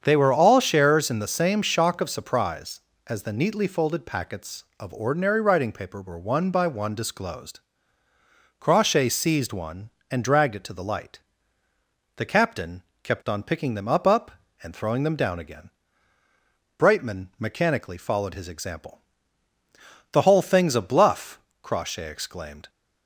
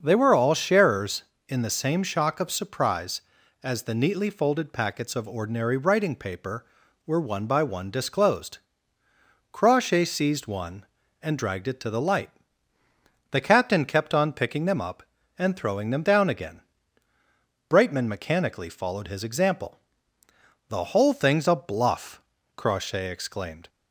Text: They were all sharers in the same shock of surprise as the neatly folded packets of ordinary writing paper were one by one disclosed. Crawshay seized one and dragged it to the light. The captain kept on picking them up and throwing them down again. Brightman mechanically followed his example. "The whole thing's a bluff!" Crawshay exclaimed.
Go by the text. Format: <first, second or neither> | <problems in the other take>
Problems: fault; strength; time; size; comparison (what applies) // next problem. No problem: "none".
second | starts louder than the rest; strong; until 1.0 s; 7.5 dB; also in the second // pauses between "captain" and "kept"; slight; at 12.8 s; 0.20 s long // says "up" twice; at 14.0 s